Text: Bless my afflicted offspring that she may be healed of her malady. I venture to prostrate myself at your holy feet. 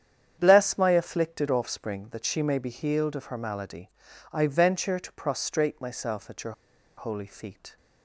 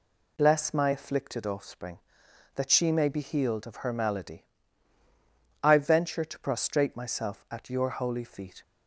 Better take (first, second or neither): second